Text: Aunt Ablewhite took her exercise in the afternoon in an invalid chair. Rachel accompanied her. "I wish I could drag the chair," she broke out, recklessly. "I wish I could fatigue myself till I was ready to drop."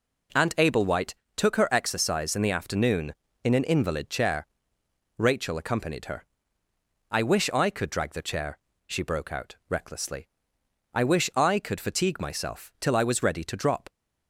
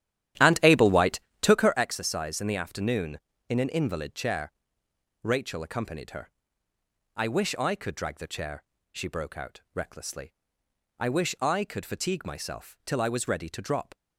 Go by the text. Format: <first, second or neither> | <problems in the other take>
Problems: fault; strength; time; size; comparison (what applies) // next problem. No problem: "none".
first | starts louder than the rest; strong; until 1.9 s; 11.5 dB // pauses between "Ablewhite" and "took"; slight; at 1.1 s; 0.22 s long; slight in the first